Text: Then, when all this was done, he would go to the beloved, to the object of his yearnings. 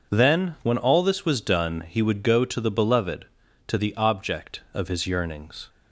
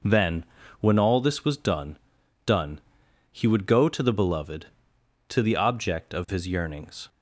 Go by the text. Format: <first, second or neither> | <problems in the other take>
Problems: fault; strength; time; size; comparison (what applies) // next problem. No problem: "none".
first | says "done" twice; at 2.4 s